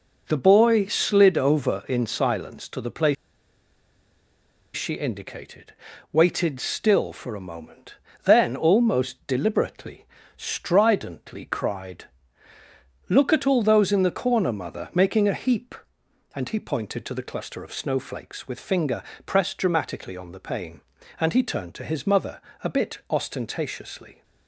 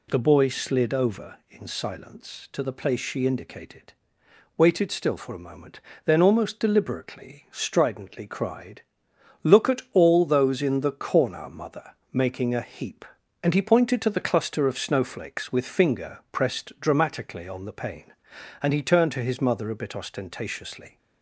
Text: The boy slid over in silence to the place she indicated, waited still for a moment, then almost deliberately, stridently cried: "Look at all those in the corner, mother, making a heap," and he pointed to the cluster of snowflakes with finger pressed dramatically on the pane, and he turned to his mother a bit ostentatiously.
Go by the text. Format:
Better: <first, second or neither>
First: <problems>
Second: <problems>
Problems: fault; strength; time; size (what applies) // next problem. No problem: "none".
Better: second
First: pauses between "place" and "she"; strong; at 3.1 s; 1.6 s long // pauses between "finger" and "pressed"; slight; at 19.0 s; 0.24 s long // pauses between "mother" and "a"; slight; at 22.4 s; 0.22 s long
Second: none